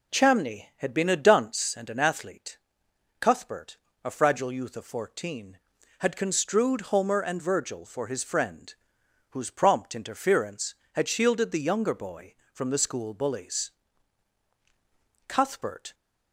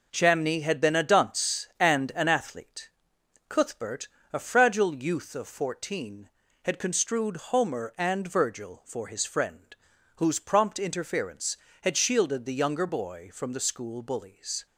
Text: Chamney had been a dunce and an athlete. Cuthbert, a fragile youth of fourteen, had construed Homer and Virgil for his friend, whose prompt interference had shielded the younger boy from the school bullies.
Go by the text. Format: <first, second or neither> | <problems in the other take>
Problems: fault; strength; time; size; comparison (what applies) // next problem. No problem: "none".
second | goes on to say "Cuthbert"; noticeable; from 15.2 s on; 0.66 s long